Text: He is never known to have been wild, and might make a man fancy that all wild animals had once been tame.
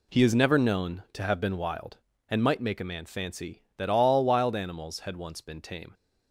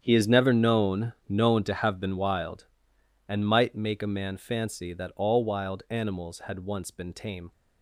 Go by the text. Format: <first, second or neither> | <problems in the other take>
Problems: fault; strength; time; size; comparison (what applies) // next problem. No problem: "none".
first | starts louder than the rest; strong; until 1.0 s; 8.5 dB // says "known" twice; at 1.2 s